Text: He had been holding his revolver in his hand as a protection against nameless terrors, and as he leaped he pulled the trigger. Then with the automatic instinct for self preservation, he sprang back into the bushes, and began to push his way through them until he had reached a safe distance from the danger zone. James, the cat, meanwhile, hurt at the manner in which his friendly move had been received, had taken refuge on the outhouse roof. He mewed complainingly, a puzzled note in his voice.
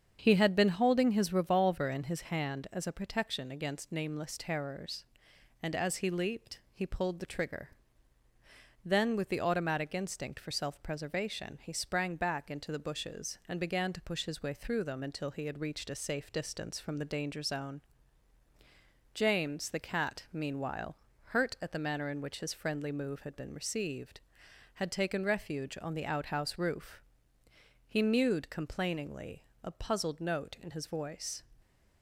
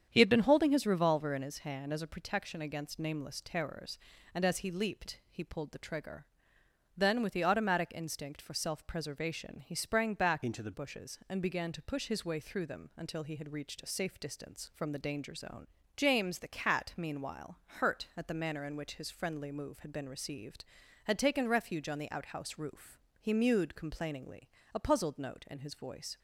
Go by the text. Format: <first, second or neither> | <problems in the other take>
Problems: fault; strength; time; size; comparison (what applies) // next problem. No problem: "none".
first | starts louder than the rest; strong; until 1.1 s; 8 dB; strong in the first // changes voice from "into" to "the"; from 10.4 to 10.7 s; 0.3 s long